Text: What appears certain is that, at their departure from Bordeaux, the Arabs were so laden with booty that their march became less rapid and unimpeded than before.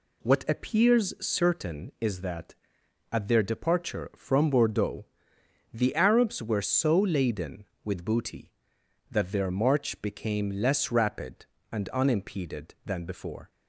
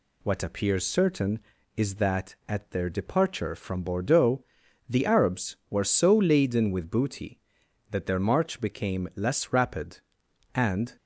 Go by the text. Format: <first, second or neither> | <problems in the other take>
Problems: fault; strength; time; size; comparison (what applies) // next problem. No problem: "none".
first | stops before "unimpeded than before"; at 10.9 s